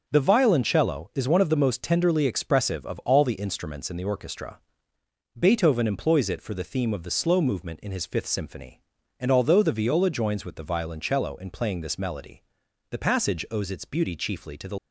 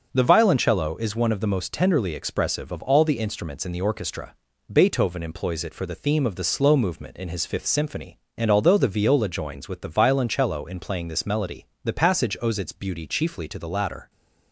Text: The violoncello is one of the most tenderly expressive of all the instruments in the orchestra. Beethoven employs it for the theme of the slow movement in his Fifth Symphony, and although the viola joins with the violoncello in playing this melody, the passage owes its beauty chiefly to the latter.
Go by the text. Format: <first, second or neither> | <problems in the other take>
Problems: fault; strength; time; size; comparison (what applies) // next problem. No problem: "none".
second | starts louder than the rest; noticeable; until 1.0 s; 6 dB; also in the second // stops before "latter"; at 14.7 s